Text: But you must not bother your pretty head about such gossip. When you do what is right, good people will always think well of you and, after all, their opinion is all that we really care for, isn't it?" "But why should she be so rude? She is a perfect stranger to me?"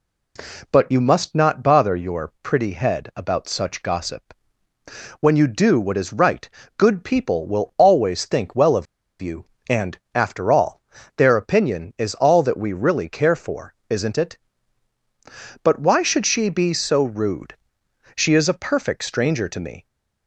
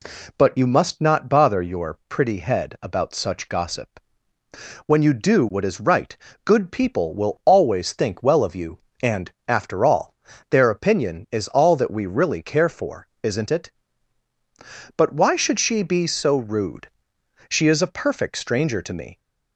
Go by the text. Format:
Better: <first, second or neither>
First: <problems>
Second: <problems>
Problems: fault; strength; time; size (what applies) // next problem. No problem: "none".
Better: second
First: pauses between "of" and "you"; slight; at 8.8 s; 0.35 s long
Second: none